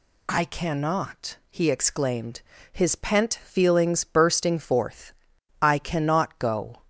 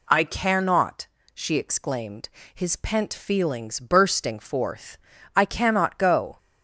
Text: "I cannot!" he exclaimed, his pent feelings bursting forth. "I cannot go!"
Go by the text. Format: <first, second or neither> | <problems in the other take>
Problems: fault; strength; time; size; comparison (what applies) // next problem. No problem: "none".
first | says "she" for "he"; at 1.3 s